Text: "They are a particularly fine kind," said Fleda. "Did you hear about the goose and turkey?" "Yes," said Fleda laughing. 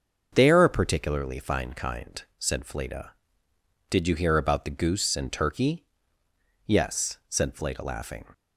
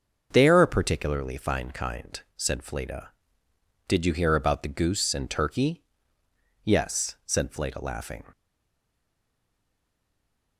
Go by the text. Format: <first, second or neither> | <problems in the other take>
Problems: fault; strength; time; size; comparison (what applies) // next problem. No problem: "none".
first | starts louder than the rest; until 1.3 s; 6.5 dB; also in the first // stays silent after the last word; from 8.3 s on; 2.2 s long